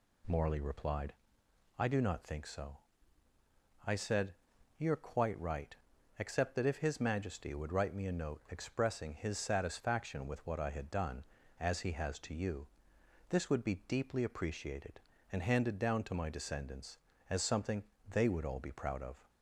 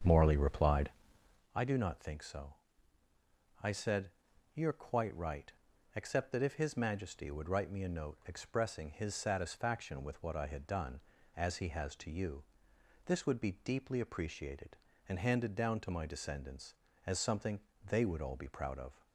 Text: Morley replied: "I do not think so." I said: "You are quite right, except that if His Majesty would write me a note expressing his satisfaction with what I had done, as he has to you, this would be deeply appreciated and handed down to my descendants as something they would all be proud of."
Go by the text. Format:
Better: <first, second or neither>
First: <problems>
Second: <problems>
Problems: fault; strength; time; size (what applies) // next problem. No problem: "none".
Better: first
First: pauses between "something" and "they"; slight; at 17.8 s; 0.24 s long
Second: starts louder than the rest; until 1.4 s; 7 dB // pauses between "something" and "they"; slight; at 17.5 s; 0.24 s long